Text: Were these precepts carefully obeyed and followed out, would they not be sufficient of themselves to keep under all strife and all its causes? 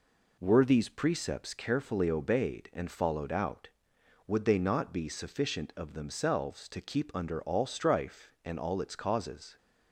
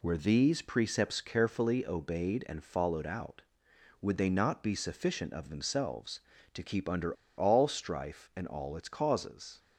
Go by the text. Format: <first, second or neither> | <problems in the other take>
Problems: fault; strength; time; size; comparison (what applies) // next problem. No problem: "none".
first | pauses between "under" and "all"; slight; at 7.1 s; 0.25 s long